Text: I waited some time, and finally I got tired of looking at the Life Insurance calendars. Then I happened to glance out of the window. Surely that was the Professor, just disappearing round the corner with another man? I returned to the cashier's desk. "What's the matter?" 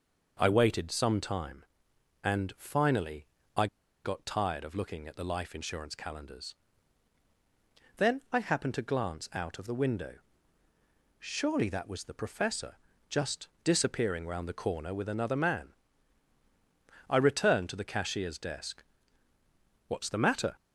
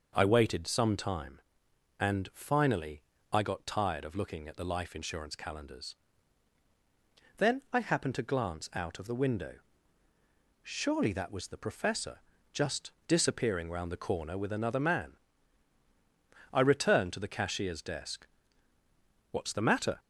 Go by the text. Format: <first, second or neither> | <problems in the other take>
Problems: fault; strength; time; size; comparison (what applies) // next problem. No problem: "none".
second | pauses between "finally" and "I"; slight; at 3.2 s; 0.30 s long; slight in the second // pauses between "I" and "got"; at 3.6 s; 0.38 s long // pauses between "just" and "disappearing"; slight; at 13.4 s; 0.16 s long; slight in the second